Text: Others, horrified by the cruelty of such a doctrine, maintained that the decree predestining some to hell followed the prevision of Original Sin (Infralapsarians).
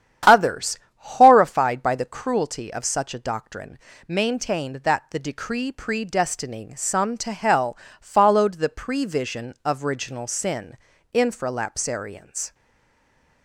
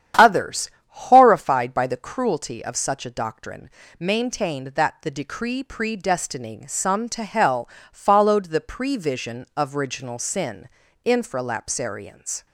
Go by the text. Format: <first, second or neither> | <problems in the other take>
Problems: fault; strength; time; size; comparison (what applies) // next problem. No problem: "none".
second | starts louder than the rest; strong; until 1.4 s; 9.5 dB; strong in the second // pauses between "hell" and "followed"; slight; at 7.7 s; 0.24 s long; slight in the second // stays silent after the last word; slight; from 12.5 s on; 0.9 s long